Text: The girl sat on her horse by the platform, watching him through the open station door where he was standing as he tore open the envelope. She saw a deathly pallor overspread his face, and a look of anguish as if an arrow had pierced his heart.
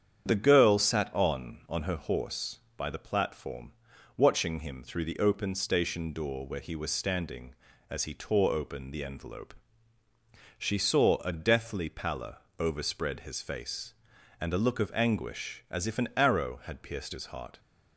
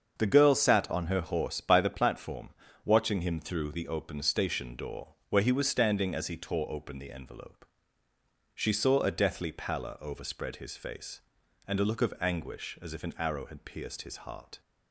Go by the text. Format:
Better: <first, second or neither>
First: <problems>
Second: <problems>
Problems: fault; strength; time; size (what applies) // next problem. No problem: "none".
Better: second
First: starts louder than the rest; strong; until 1.3 s; 8.5 dB // says "on" twice; at 1.6 s // pauses between "pallor" and "overspread"; slight; at 12.3 s; 0.20 s long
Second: starts louder than the rest; until 1.1 s; 7 dB